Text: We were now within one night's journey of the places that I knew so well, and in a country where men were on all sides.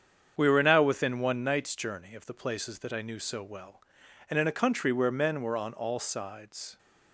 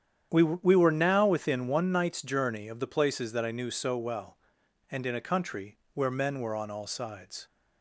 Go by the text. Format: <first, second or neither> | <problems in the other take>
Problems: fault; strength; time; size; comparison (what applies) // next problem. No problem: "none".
first | starts louder than the rest; strong; until 1.3 s; 9 dB; strong in the first // says "We" twice; at 0.4 s // pauses between "country" and "where"; slight; at 5.7 s; 0.16 s long